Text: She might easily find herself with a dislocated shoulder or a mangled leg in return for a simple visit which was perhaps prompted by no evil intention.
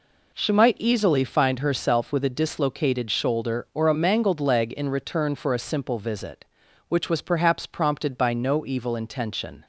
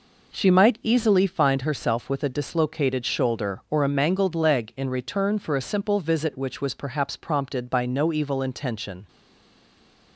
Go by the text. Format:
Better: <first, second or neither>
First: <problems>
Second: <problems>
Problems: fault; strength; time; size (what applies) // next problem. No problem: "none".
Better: first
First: none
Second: stays silent after the last word; from 9.0 s on; 1.1 s long